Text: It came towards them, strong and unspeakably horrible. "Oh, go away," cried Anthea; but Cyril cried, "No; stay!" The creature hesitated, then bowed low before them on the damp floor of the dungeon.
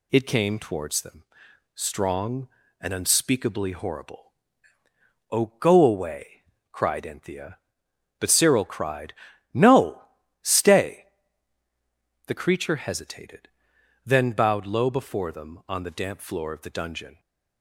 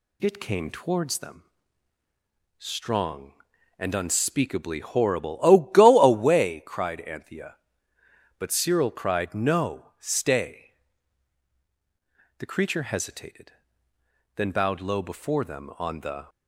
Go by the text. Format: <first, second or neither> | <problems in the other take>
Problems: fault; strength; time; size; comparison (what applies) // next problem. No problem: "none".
first | stops before "damp floor of the dungeon"; at 16.2 s